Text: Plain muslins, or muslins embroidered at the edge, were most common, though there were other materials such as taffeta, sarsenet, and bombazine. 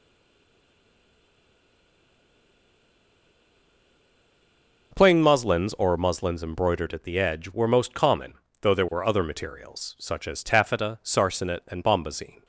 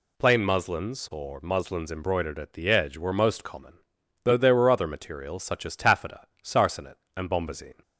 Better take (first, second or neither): second